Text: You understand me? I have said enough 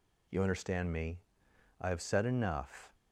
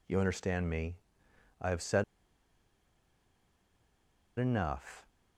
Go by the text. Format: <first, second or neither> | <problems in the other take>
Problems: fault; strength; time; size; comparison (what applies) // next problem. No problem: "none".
first | pauses between "said" and "enough"; strong; at 2.0 s; 2.3 s long